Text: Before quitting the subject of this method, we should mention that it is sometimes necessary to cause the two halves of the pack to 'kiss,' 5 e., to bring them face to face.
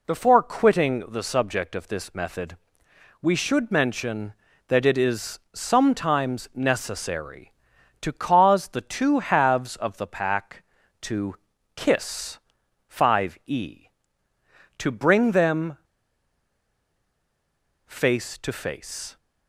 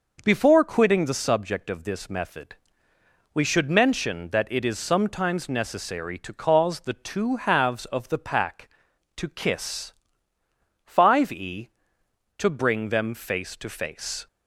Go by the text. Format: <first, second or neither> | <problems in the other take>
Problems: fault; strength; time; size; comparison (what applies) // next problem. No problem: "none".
second | pauses between "is" and "sometimes"; slight; at 5.3 s; 0.16 s long // pauses between "to" and "kiss"; at 11.3 s; 0.40 s long // pauses between "them" and "face"; strong; at 15.7 s; 2.0 s long